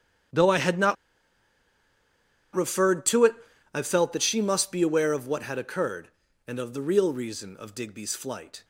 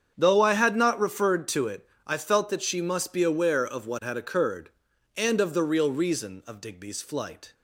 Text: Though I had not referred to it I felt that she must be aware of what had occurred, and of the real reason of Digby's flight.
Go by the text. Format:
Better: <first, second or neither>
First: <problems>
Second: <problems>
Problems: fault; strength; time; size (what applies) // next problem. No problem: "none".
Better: second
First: starts louder than the rest; strong; until 2.9 s; 9.5 dB // pauses between "not" and "referred"; strong; at 0.9 s; 1.5 s long // pauses between "it" and "I"; at 3.3 s; 0.38 s long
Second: starts louder than the rest; strong; until 1.1 s; 7.5 dB // pauses between "it" and "I"; slight; at 1.8 s; 0.18 s long